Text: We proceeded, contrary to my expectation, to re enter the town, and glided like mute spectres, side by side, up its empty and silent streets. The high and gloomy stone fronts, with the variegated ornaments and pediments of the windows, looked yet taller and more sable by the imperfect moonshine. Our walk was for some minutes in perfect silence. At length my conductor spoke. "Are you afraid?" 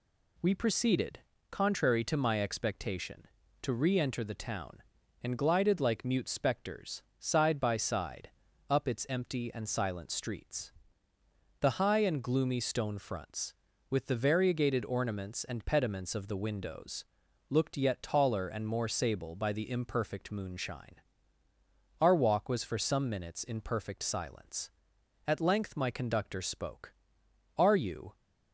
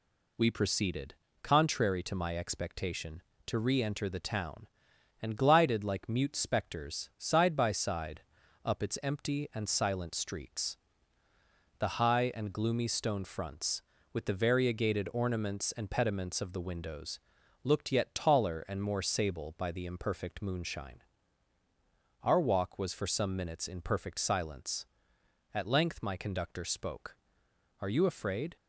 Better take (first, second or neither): second